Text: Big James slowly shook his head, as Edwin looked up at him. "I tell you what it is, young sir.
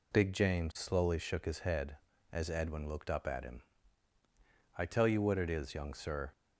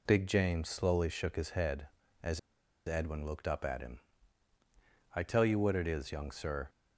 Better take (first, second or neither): first